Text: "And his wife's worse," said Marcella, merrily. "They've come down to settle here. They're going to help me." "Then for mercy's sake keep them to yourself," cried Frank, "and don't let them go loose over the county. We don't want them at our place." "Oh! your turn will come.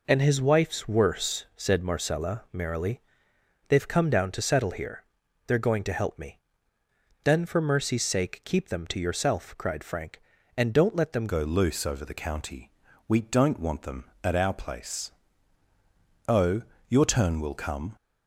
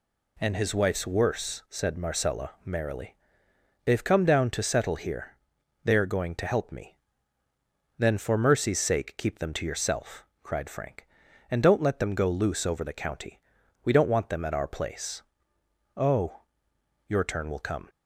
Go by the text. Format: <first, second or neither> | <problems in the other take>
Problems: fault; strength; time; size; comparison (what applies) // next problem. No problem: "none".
second | changes voice at "go"; from 11.2 s on; 6.7 s long